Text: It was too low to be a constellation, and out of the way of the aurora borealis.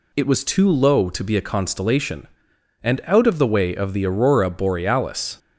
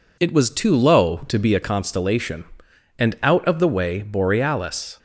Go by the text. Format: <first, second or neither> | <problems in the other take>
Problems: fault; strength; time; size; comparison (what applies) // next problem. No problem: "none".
first | skips "of the aurora"; at 4.0 s